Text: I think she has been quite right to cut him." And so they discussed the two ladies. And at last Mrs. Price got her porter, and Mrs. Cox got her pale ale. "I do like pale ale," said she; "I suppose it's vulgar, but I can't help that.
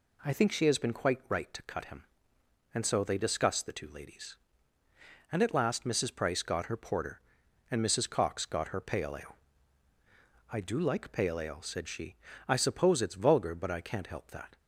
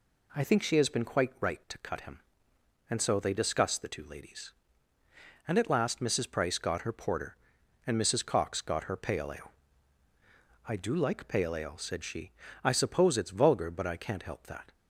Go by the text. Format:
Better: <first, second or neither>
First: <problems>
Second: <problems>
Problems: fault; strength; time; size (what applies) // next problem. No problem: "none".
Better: neither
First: none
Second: none